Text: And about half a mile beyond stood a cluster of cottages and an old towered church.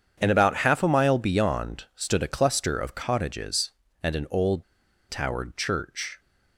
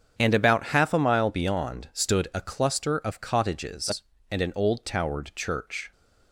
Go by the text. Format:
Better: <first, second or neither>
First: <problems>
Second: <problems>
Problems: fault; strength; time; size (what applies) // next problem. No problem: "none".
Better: second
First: starts louder than the rest; strong; until 1.2 s; 8 dB // pauses between "old" and "towered"; noticeable; at 4.6 s; 0.47 s long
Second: starts louder than the rest; strong; until 1.1 s; 7.5 dB